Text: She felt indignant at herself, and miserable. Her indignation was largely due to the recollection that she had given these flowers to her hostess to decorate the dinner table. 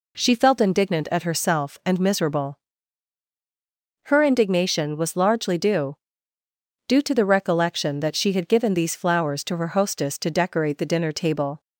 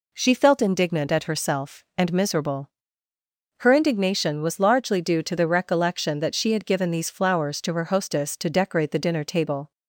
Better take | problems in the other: second | says "due" twice; at 6.8 s

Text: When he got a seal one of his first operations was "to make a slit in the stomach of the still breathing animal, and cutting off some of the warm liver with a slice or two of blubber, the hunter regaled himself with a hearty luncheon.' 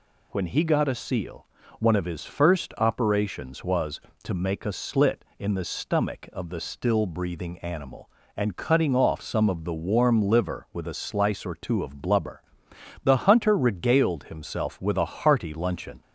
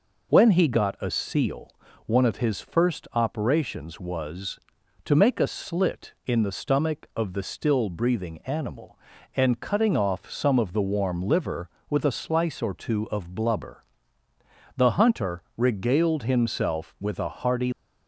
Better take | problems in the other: first | pauses between "seal" and "one"; slight; at 1.7 s; 0.34 s long; slight in the first // stops before "luncheon"; at 17.7 s

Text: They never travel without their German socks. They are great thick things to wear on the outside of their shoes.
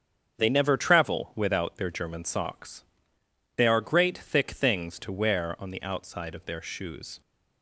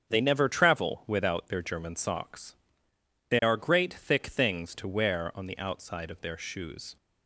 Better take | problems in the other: neither | starts louder than the rest; strong; the same in both

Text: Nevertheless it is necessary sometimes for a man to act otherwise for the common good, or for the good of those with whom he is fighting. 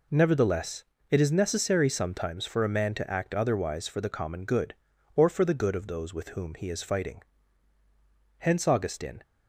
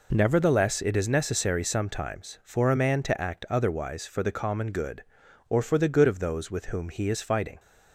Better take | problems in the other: second | pauses between "Nevertheless" and "it"; slight; at 0.8 s; 0.26 s long // goes on to say "Hence Augustine"; noticeable; from 8.3 s on; 0.84 s long

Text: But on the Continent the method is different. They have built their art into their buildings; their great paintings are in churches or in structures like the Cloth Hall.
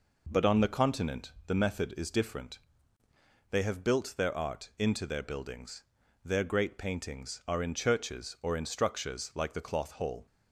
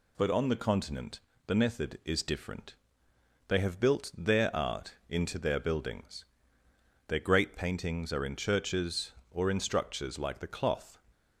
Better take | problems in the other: first | pauses between "Continent" and "the"; slight; at 1.1 s; 0.26 s long // stops before "Hall"; at 11.1 s

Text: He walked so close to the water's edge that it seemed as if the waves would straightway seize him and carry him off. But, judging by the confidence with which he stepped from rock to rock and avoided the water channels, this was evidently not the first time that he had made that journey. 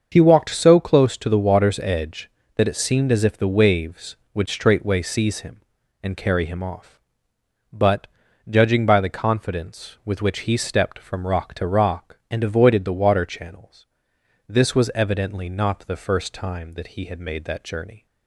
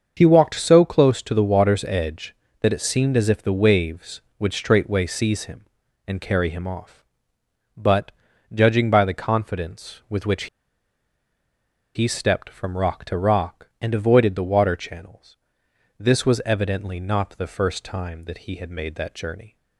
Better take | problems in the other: first | starts louder than the rest; until 1.1 s; 6.5 dB; also in the first // pauses between "which" and "he"; strong; at 10.4 s; 1.4 s long

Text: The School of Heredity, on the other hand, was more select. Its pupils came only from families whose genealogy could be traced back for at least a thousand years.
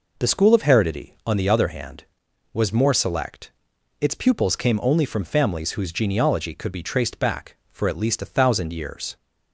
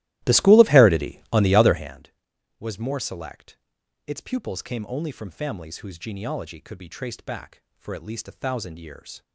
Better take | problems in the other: first | starts louder than the rest; strong; until 2.0 s; 16 dB

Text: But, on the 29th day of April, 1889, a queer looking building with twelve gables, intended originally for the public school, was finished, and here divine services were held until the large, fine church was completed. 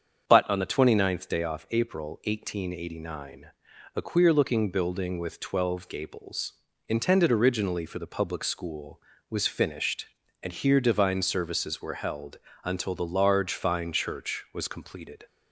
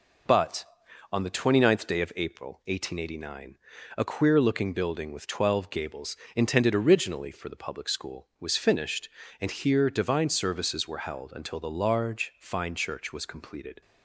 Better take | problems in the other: second | starts louder than the rest; strong; until 1.2 s; 7 dB // says "off" for "of"; at 1.4 s // pauses between "held" and "until"; slight; at 12.3 s; 0.26 s long

